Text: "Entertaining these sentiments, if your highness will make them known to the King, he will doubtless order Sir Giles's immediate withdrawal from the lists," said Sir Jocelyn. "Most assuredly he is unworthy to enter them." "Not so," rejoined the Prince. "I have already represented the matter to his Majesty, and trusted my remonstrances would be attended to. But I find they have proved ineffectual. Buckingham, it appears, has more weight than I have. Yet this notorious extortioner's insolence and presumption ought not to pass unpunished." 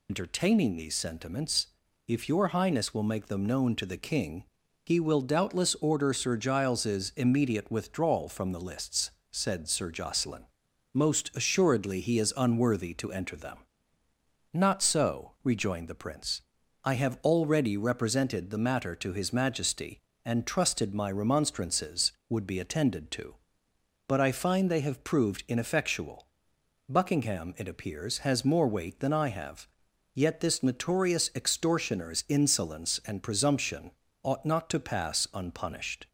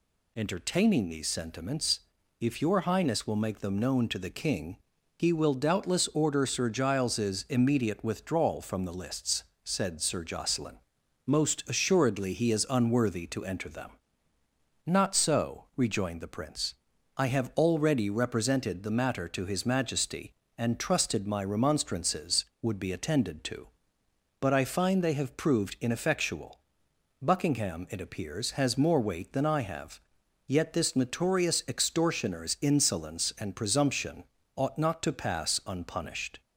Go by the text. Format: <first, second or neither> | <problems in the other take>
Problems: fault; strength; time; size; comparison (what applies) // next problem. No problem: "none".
second | loses the start of "Entertaining"; at 0.0 s; 70 ms // pauses between "presumption" and "ought"; slight; at 33.9 s; 0.32 s long; slight in the second